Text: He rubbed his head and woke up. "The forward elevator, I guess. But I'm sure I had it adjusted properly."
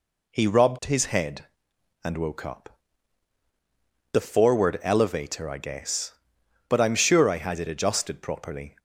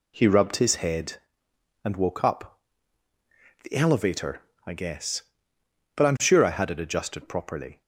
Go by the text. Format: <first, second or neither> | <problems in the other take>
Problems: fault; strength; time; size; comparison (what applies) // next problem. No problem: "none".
first | skips "forward"; at 3.7 s